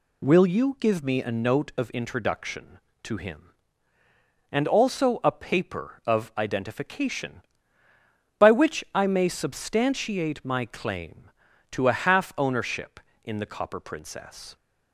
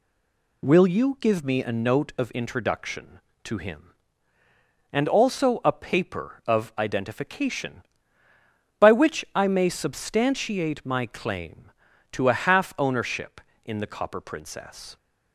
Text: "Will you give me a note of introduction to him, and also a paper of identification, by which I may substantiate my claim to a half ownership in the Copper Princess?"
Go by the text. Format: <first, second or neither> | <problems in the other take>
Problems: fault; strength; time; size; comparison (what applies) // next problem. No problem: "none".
first | stays silent before the first word; slight; until 0.6 s; 0.6 s long